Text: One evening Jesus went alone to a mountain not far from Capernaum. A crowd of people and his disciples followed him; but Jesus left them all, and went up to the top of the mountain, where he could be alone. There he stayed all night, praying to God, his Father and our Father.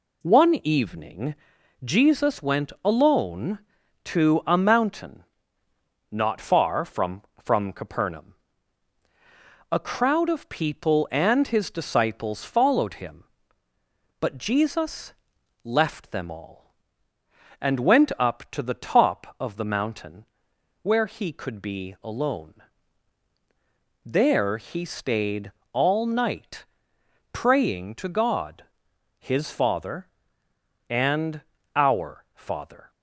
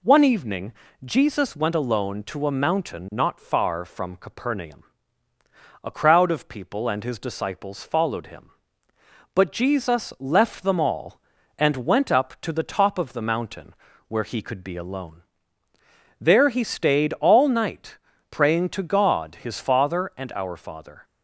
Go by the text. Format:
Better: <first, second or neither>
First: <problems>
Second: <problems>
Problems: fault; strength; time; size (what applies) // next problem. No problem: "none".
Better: second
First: pauses between "evening" and "Jesus"; noticeable; at 1.3 s; 0.50 s long // pauses between "mountain" and "not"; noticeable; at 5.2 s; 0.88 s long // says "from" twice; at 7.4 s // pauses between "Jesus" and "left"; noticeable; at 15.1 s; 0.52 s long // pauses between "stayed" and "all"; slight; at 25.4 s; 0.22 s long // pauses between "and" and "our"; slight; at 31.4 s; 0.34 s long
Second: pauses between "evening" and "Jesus"; slight; at 0.7 s; 0.30 s long